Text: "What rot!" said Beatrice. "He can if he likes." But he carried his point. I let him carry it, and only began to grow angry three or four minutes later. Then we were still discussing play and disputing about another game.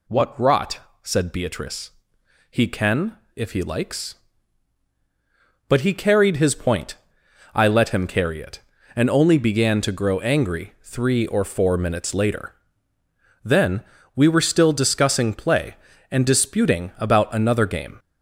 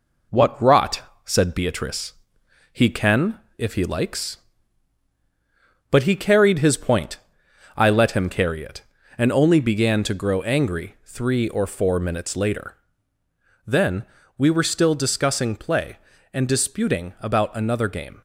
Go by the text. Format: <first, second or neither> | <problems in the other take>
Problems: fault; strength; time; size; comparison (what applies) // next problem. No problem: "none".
first | gets quieter; slight; throughout; 3.5 dB // pauses between "can" and "if"; slight; at 3.3 s; 0.18 s long; slight in the first // pauses between "Then" and "we"; slight; at 14.0 s; 0.32 s long; slight in the first